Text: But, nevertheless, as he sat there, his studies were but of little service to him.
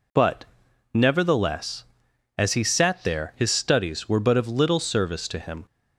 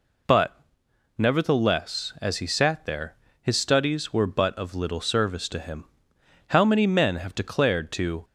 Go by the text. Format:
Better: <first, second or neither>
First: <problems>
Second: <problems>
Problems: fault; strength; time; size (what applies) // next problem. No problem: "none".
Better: first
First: none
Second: goes on to say "How many men have declared to"; strong; from 6.4 s on; 1.7 s long